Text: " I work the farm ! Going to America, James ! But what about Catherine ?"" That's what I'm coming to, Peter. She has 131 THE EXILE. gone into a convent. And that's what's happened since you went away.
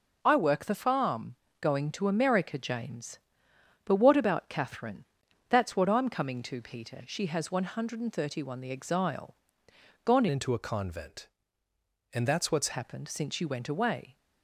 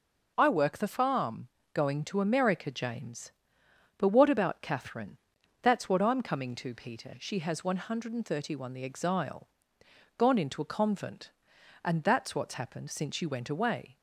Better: second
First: changes voice from "into" to "what's"; from 10.2 to 12.7 s; 2.5 s long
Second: none

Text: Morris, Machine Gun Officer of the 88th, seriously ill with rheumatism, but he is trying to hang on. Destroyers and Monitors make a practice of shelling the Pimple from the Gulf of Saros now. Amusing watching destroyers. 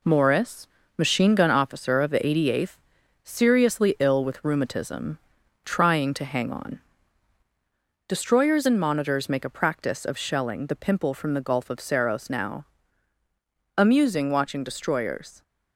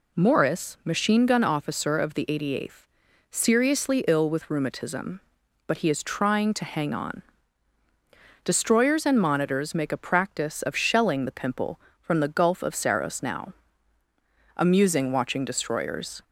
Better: second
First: skips "but he is"; at 5.4 s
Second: none

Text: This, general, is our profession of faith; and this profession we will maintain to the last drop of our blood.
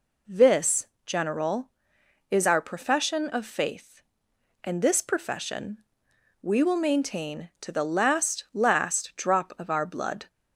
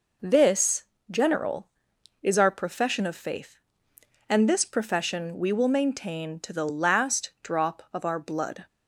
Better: second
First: pauses between "profession" and "we"; noticeable; at 5.7 s; 0.62 s long // says "last" twice; at 8.5 s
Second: none

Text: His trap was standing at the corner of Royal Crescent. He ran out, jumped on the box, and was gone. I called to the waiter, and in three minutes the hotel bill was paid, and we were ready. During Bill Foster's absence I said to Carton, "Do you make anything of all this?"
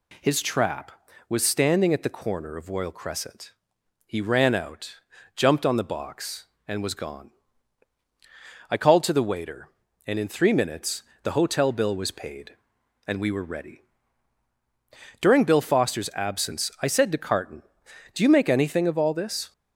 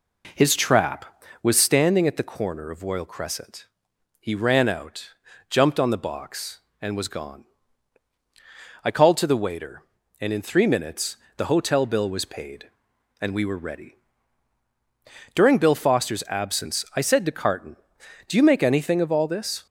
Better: first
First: pauses between "minutes" and "the"; slight; at 11.0 s; 0.20 s long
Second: starts louder than the rest; until 1.9 s; 3.5 dB // pauses between "minutes" and "the"; slight; at 11.1 s; 0.20 s long

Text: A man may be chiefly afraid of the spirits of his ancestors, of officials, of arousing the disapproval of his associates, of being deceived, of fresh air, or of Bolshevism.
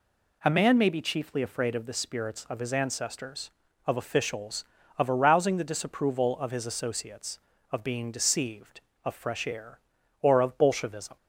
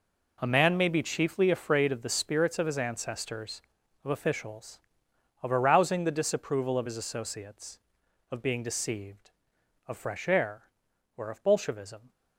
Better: first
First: none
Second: gets quieter; strong; throughout; 13 dB

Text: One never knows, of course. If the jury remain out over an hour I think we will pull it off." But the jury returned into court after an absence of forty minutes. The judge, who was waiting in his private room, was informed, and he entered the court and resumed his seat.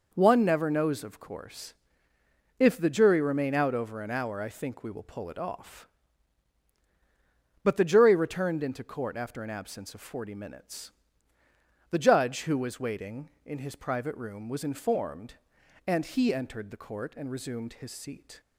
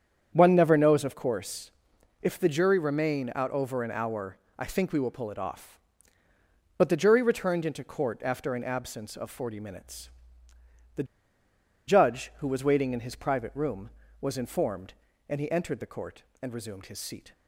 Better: first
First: none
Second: starts louder than the rest; strong; until 1.3 s; 8 dB // pauses between "hour" and "I"; slight; at 4.3 s; 0.20 s long // pauses between "The" and "judge"; noticeable; at 11.0 s; 0.83 s long

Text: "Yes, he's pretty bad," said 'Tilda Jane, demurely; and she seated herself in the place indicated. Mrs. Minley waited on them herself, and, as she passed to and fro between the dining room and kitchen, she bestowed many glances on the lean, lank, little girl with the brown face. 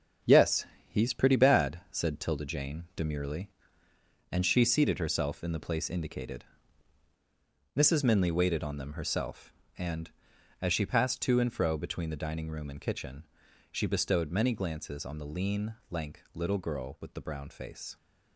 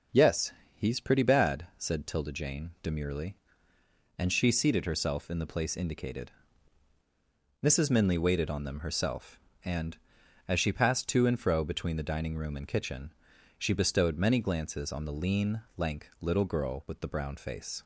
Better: second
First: gets quieter; throughout; 7 dB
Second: none

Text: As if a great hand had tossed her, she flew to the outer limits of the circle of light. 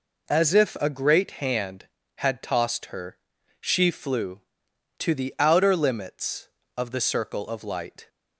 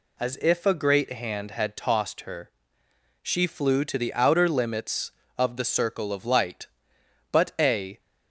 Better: first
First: none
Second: goes on to say "But a"; noticeable; from 7.3 s on; 0.68 s long

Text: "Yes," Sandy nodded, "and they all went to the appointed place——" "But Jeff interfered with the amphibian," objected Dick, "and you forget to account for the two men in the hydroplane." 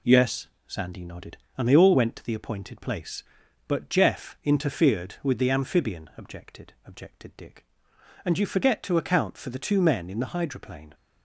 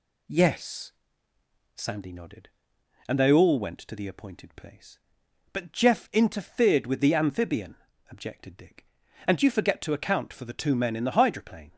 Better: second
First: says "objected" twice; at 6.8 s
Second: none

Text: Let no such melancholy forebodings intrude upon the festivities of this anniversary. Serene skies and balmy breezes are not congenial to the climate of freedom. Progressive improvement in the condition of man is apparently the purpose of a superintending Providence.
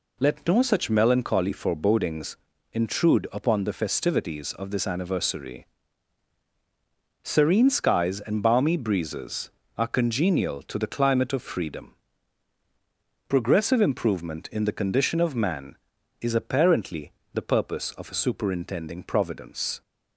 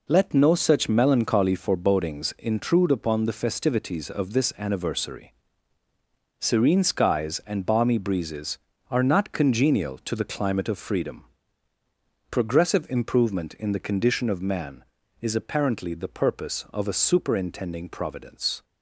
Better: second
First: pauses between "forebodings" and "intrude"; slight; at 2.3 s; 0.36 s long // skips "not"; at 9.8 s // pauses between "apparently" and "the"; slight; at 17.1 s; 0.22 s long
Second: none

